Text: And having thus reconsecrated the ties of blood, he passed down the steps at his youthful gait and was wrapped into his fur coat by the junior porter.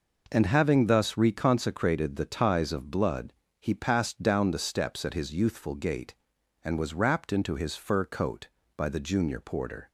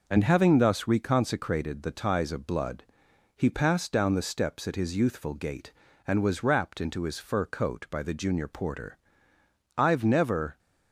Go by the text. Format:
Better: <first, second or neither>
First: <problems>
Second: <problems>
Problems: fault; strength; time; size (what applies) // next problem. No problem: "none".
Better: first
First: none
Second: goes on to say "I've never"; noticeable; from 9.7 s on; 0.82 s long